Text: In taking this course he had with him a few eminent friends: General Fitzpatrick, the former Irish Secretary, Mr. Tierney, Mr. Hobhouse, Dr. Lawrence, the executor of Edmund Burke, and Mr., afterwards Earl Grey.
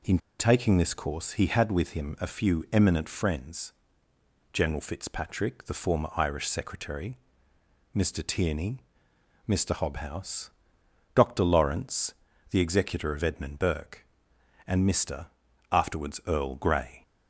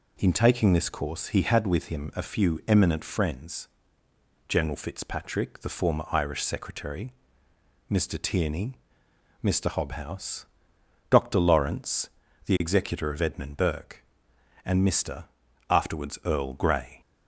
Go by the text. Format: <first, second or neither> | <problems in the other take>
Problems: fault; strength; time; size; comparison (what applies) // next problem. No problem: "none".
second | pauses between "In" and "taking"; slight; at 0.1 s; 0.21 s long